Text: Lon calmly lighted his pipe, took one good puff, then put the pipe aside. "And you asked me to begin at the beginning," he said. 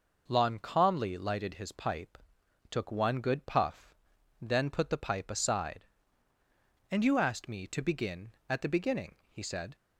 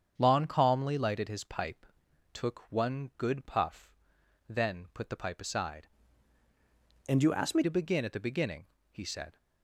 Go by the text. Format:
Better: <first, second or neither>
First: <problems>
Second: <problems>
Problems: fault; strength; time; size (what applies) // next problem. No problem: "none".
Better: first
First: none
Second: starts louder than the rest; strong; until 1.1 s; 7.5 dB // changes voice from "And" to "me"; from 7.0 to 7.6 s; 0.6 s long